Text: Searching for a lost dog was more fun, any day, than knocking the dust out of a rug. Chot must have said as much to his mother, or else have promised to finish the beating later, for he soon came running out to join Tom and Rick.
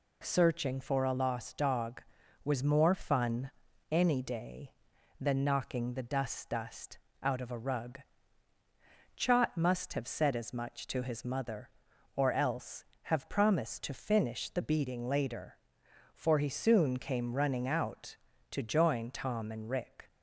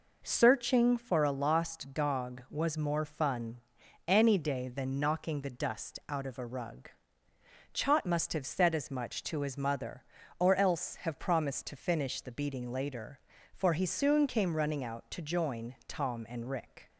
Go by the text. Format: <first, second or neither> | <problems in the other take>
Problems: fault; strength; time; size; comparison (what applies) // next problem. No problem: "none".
second | says "dust" twice; at 6.4 s